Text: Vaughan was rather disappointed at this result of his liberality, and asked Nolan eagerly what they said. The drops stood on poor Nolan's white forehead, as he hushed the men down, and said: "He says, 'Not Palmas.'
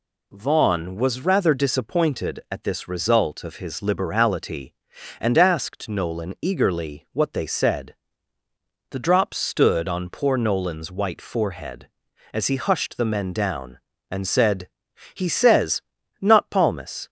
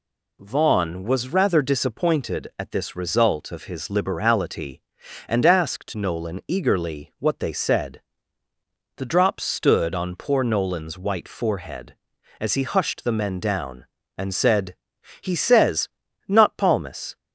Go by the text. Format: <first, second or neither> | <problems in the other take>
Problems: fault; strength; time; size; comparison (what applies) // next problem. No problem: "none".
neither | none